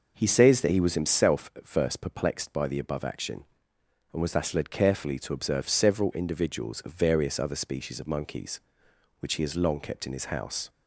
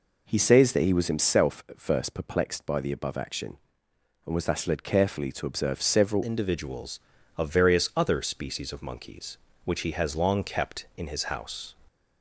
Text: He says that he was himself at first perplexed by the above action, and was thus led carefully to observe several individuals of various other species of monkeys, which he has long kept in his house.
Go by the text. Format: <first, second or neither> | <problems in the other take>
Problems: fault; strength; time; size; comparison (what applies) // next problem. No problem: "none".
first | changes voice at "individuals"; from 6.2 s on; 5.5 s long